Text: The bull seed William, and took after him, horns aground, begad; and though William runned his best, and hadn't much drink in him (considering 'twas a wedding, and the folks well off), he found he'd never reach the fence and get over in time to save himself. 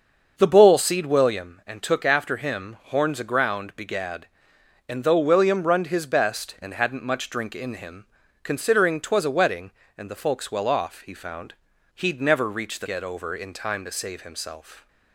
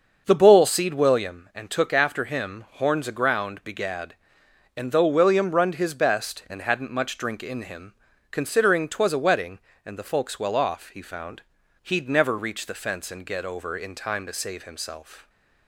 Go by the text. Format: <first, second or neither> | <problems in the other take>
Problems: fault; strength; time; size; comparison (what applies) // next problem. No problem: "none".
second | starts louder than the rest; until 1.3 s; 6.5 dB; also in the second // pauses between "found" and "he'd"; at 11.5 s; 0.42 s long; also in the second // skips "fence and"; at 12.8 s